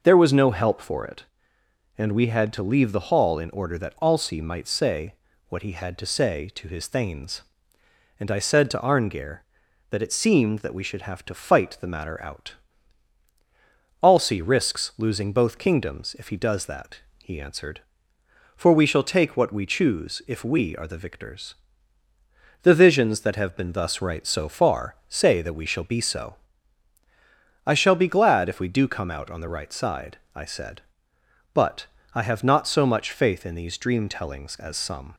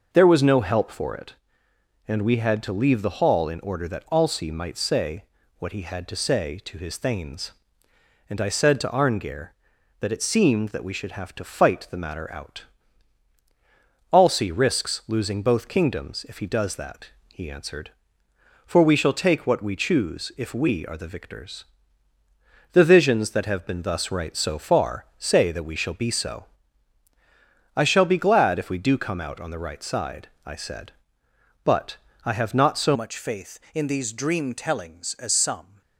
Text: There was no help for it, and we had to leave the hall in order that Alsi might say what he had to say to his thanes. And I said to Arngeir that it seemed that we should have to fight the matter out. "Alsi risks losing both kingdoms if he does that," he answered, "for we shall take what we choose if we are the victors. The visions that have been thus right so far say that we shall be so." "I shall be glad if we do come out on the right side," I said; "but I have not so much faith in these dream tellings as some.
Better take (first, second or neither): first